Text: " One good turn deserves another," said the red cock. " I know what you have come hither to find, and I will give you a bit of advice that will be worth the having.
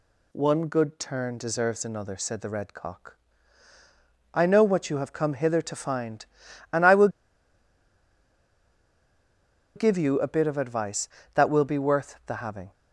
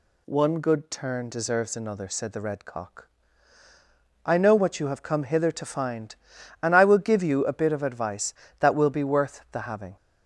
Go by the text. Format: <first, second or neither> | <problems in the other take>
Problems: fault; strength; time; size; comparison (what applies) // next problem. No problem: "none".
second | pauses between "will" and "give"; strong; at 7.0 s; 2.6 s long